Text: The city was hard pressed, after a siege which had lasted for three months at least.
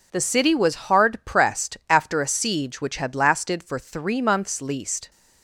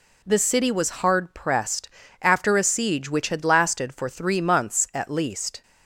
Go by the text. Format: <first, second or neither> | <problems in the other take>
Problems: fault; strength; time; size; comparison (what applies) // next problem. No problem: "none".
second | skips "at"; at 4.6 s